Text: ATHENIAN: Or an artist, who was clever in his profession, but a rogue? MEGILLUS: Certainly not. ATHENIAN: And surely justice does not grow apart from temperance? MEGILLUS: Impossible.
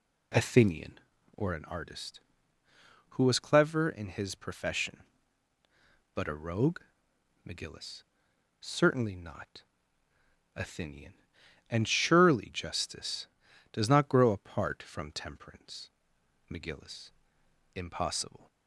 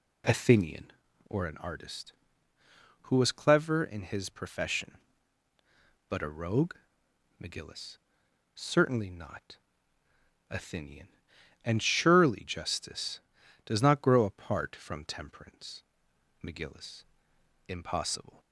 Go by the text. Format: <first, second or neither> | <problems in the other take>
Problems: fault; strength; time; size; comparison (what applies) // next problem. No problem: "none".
neither | none